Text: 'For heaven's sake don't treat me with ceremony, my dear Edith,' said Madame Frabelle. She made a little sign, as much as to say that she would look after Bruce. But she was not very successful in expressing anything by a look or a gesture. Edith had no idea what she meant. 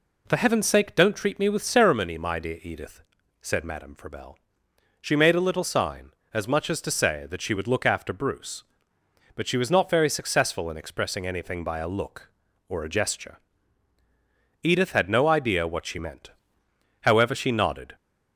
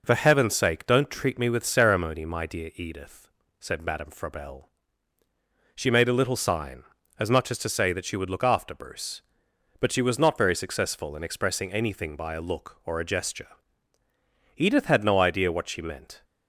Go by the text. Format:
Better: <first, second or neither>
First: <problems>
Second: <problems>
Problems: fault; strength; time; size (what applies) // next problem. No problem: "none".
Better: second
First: goes on to say "However she nodded"; noticeable; from 17.0 s on; 0.94 s long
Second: none